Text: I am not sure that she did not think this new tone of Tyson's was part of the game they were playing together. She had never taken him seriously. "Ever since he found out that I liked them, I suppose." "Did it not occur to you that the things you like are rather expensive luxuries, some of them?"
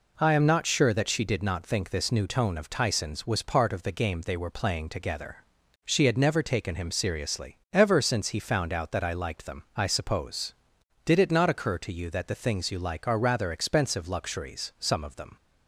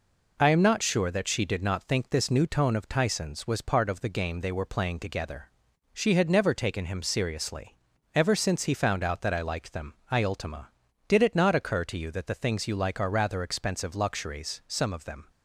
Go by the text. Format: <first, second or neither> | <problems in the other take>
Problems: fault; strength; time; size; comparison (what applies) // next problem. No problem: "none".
first | says "ultima" for "suppose"; at 10.2 s